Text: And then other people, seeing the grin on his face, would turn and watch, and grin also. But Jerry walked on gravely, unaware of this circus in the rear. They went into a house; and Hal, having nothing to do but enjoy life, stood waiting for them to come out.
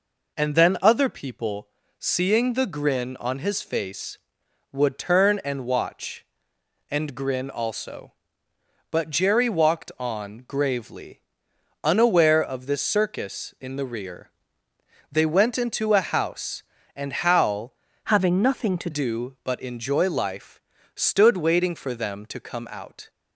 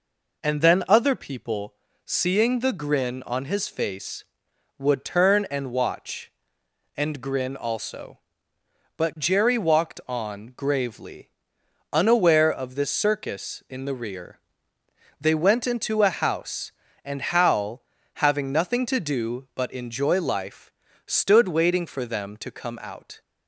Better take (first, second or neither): second